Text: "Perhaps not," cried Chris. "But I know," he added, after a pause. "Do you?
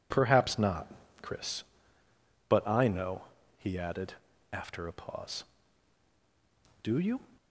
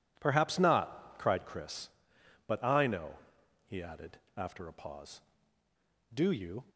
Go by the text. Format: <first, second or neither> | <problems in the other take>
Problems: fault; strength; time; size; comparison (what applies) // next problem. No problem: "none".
second | skips "cried"; at 1.0 s